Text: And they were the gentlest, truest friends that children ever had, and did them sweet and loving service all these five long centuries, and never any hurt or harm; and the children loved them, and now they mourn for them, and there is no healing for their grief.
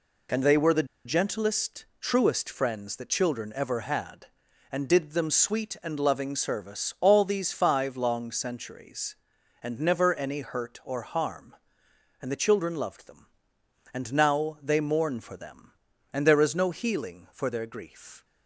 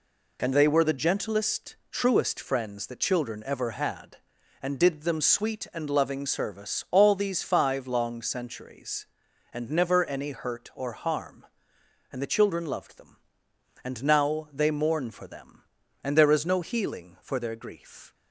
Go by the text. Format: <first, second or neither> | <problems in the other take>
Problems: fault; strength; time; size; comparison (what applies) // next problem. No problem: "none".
second | pauses between "the" and "gentlest"; slight; at 0.8 s; 0.20 s long